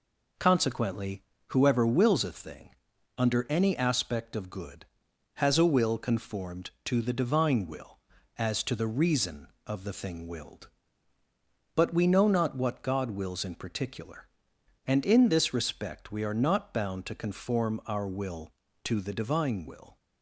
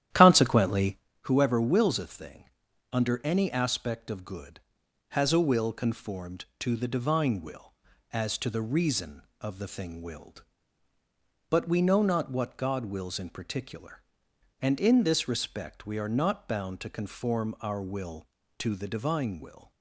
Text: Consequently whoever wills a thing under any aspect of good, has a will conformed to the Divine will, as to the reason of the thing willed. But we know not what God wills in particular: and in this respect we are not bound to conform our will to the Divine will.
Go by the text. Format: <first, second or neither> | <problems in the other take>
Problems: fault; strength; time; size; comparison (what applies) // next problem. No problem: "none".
first | starts louder than the rest; strong; until 1.0 s; 11.5 dB // pauses between "Consequently" and "whoever"; slight; at 0.9 s; 0.26 s long; slight in the first // pauses between "thing" and "under"; noticeable; at 2.4 s; 0.48 s long; noticeable in the first